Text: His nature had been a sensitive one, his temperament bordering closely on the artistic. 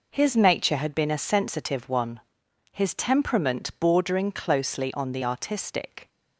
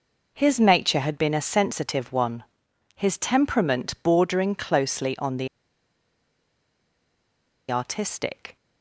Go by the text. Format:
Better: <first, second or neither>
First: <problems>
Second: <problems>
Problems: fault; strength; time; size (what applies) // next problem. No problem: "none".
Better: first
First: none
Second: pauses between "the" and "artistic"; strong; at 5.4 s; 2.2 s long